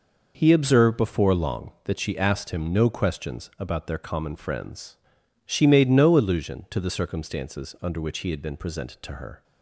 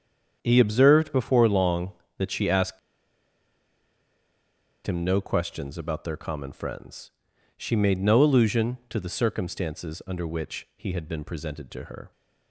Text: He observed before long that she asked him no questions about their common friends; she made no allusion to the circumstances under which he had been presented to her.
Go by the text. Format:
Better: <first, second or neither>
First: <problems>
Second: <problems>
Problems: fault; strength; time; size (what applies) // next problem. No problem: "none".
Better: first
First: none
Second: starts louder than the rest; strong; until 1.4 s; 8 dB // pauses between "asked" and "him"; strong; at 2.7 s; 2.0 s long